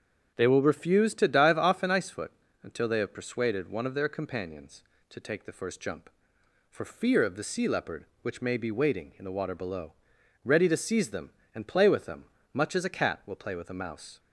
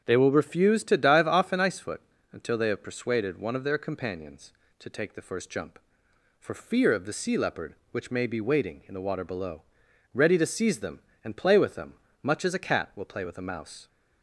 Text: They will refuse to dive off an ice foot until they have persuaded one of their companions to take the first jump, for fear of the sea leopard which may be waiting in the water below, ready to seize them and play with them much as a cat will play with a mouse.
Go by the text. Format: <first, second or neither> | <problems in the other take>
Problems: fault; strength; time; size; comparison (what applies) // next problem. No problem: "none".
neither | starts louder than the rest; strong; the same in both // pauses between "foot" and "until"; slight; the same in both // pauses between "them" and "much"; slight; the same in both